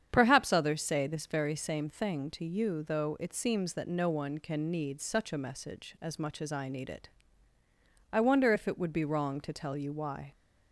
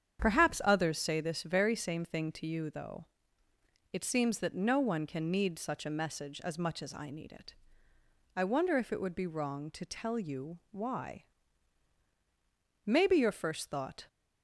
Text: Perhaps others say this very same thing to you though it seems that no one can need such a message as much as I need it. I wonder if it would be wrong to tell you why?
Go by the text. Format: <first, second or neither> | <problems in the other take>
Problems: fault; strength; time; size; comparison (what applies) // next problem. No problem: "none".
first | starts louder than the rest; strong; until 1.2 s; 8 dB; strong in the first // pauses between "though" and "it"; noticeable; at 3.0 s; 0.86 s long // goes on to say "Maybe your first thought"; noticeable; from 12.8 s on; 1.2 s long